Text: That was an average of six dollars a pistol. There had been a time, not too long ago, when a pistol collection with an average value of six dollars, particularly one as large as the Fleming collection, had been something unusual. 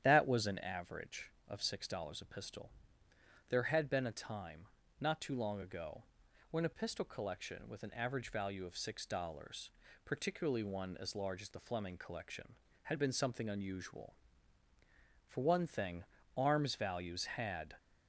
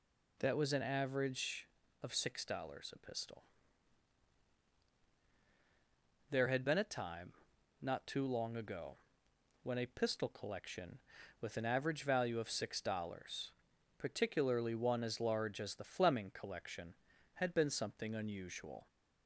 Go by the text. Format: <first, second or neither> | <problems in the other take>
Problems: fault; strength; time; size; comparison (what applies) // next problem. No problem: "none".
second | starts louder than the rest; strong; until 1.0 s; 10 dB // goes on to say "For one thing arms values had"; strong; from 15.2 s on; 2.4 s long